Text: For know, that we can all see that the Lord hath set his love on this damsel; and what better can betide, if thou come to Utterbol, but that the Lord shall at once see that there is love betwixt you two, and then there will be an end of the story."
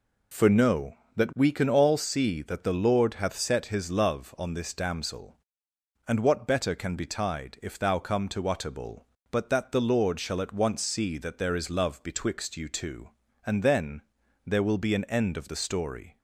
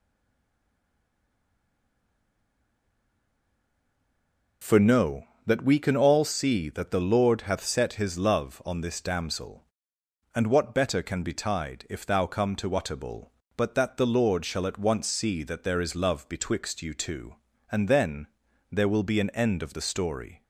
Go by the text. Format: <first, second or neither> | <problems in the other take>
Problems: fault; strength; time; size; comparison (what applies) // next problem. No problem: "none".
first | stays silent before the first word; strong; until 4.6 s; 4.6 s long // pauses between "then" and "there"; at 18.2 s; 0.44 s long; also in the first